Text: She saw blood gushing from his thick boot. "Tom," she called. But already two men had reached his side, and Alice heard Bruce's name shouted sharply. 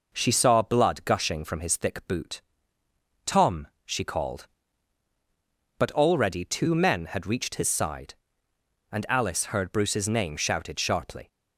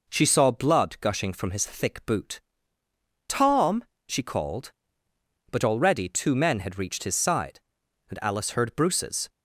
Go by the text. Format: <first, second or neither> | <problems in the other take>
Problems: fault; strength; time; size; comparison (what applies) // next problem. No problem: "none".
first | stops before "name shouted sharply"; at 9.2 s